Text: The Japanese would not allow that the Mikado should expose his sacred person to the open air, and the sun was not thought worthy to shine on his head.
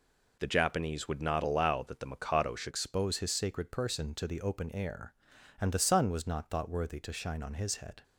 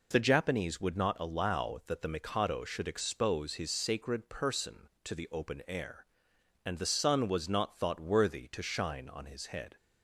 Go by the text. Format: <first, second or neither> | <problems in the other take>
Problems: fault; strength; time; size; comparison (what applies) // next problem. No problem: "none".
second | changes voice at "expose"; from 2.6 s on; 5.4 s long